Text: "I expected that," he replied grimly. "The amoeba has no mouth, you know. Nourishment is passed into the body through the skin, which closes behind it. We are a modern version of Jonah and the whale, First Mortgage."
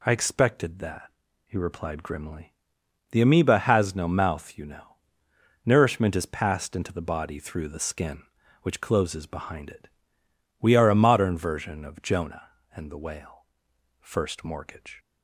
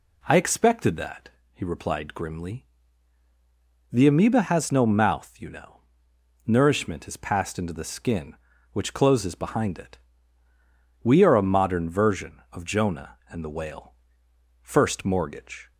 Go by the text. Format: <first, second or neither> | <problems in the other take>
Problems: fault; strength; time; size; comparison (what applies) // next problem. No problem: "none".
first | skips "the body through"; at 7.7 s